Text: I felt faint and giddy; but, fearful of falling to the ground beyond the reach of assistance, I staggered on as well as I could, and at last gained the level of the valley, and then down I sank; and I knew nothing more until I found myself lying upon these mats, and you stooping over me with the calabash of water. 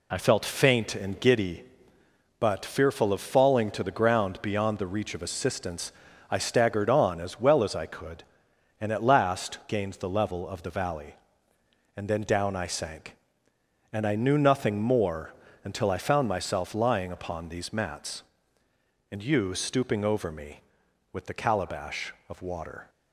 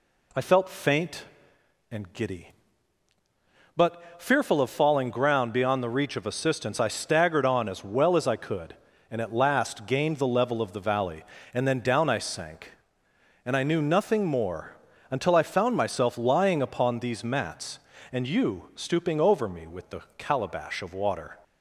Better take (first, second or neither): first